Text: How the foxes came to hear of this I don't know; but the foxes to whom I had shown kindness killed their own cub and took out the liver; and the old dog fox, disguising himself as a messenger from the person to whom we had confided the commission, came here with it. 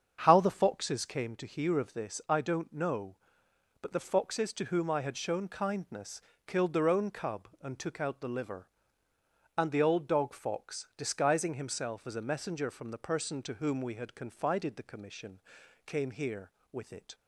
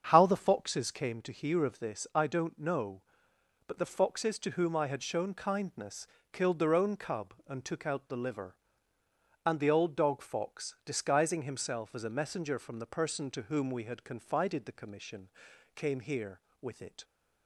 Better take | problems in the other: neither | starts louder than the rest; strong; the same in both // pauses between "kindness" and "killed"; slight; the same in both

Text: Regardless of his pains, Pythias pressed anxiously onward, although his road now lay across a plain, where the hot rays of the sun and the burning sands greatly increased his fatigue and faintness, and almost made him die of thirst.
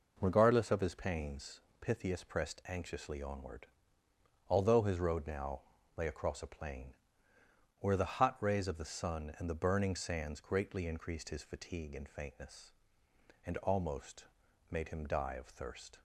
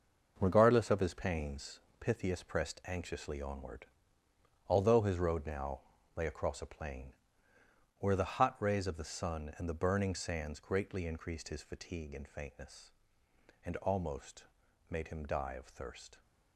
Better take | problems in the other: first | gets quieter; strong; throughout; 8.5 dB // pauses between "now" and "lay"; slight; at 5.8 s; 0.34 s long; slight in the first // pauses between "almost" and "made"; noticeable; at 14.4 s; 0.48 s long; noticeable in the first

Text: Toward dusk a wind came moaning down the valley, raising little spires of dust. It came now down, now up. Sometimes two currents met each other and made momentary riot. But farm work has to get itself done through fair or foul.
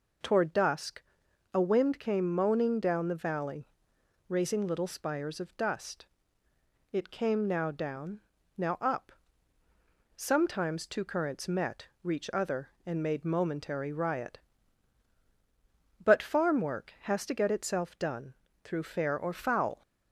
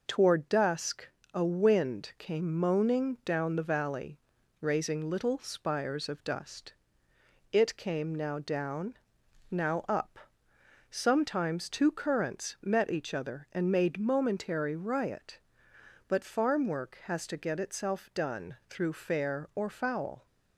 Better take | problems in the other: second | pauses between "dusk" and "a"; noticeable; at 1.0 s; 0.52 s long; slight in the second // says "reach" for "each"; at 12.0 s // pauses between "done" and "through"; slight; at 18.3 s; 0.30 s long

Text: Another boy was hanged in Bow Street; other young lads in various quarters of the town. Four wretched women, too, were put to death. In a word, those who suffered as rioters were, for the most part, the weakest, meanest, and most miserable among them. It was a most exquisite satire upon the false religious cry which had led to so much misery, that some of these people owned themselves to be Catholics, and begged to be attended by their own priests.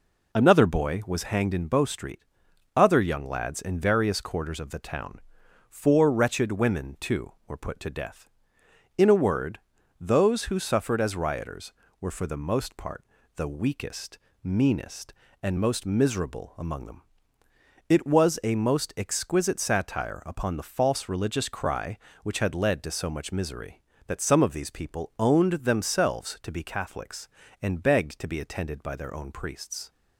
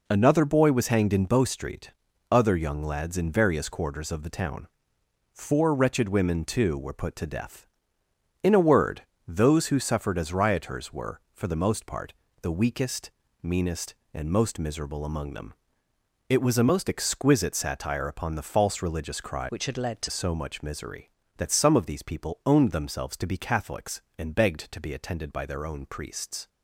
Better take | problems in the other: first | changes voice from "which" to "to"; from 19.4 to 20.0 s; 0.6 s long

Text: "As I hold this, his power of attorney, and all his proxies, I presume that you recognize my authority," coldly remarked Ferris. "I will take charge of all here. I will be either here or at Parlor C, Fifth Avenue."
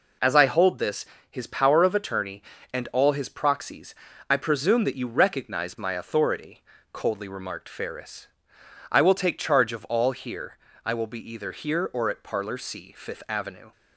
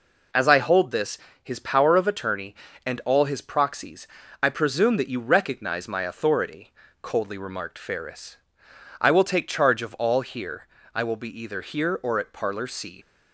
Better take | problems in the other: first | stops before "Fifth Avenue"; at 13.0 s

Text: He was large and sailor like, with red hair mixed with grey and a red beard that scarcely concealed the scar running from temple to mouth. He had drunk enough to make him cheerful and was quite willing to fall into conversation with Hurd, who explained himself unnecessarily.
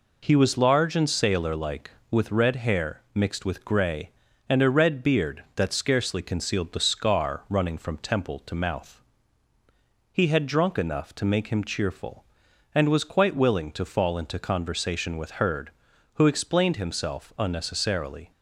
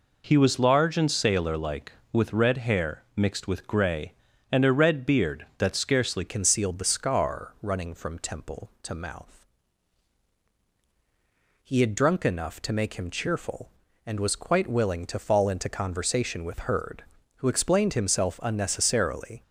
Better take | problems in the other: first | changes voice at "concealed"; from 6.2 s on; 13.2 s long

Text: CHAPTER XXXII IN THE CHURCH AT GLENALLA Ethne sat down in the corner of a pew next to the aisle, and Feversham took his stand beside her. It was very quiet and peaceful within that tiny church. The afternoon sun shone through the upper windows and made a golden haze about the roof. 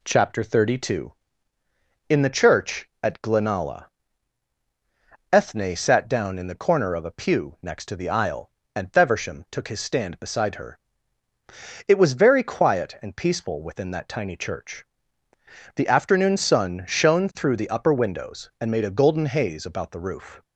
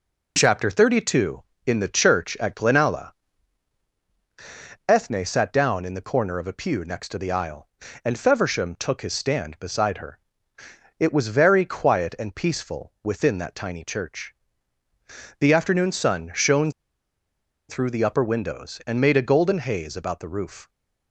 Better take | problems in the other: first | pauses between "GLENALLA" and "Ethne"; strong; at 3.1 s; 1.7 s long; strong in the first // pauses between "shone" and "through"; noticeable; at 16.7 s; 0.97 s long

